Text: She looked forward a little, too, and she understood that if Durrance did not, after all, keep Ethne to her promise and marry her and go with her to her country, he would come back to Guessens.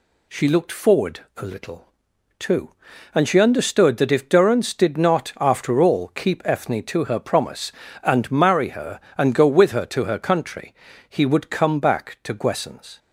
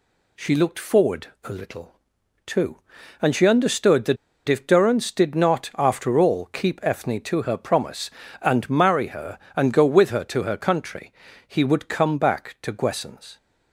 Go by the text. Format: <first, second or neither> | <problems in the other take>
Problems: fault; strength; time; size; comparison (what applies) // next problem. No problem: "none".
first | pauses between "forward" and "a"; slight; at 1.2 s; 0.18 s long; slight in the first // pauses between "that" and "if"; slight; at 4.1 s; 0.32 s long